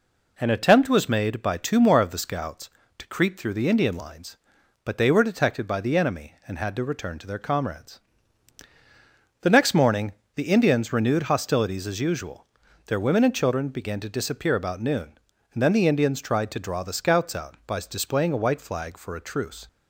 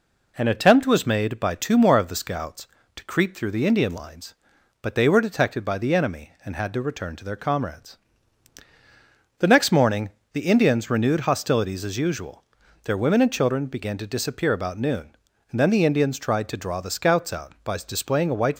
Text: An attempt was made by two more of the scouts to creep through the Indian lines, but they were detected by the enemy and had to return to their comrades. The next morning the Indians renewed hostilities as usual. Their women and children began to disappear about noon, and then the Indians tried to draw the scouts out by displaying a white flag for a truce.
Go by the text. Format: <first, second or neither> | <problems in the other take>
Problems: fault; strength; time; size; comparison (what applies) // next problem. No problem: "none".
first | pauses between "morning" and "the"; slight; at 10.1 s; 0.22 s long; slight in the first // stops before "flag for a truce"; at 18.5 s